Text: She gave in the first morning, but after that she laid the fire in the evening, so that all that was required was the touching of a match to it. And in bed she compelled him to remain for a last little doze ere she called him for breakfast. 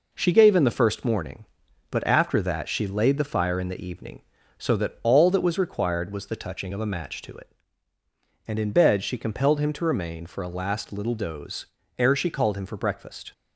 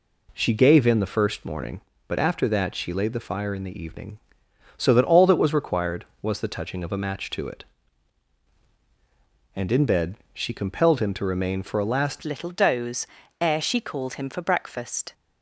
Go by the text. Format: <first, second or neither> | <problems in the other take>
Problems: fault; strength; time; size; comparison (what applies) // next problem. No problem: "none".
first | pauses between "bed" and "she"; slight; at 10.1 s; 0.16 s long // changes voice at "little"; from 12.2 s on; 2.9 s long // pauses between "doze" and "ere"; slight; at 13.0 s; 0.34 s long; slight in the first